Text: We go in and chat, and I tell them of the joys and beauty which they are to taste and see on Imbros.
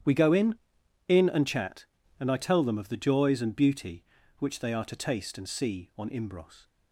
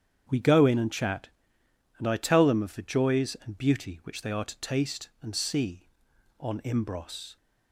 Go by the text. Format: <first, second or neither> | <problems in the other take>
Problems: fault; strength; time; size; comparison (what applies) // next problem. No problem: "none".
second | starts louder than the rest; strong; until 1.5 s; 10 dB; strong in the second // says "in" twice; at 1.0 s